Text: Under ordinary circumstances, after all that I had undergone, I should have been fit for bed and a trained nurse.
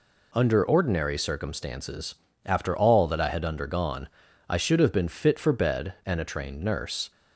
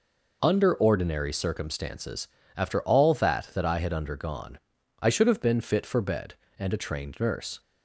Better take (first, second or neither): first